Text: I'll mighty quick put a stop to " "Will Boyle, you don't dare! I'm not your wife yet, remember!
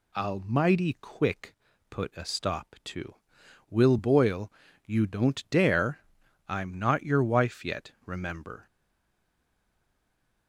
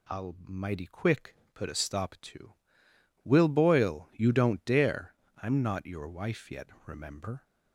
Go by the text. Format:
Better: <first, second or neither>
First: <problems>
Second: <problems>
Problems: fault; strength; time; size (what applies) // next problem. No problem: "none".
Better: second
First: pauses between "quick" and "put"; slight; at 1.5 s; 0.34 s long // stays silent after the last word; noticeable; from 8.6 s on; 1.8 s long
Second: pauses between "quick" and "put"; slight; at 1.3 s; 0.18 s long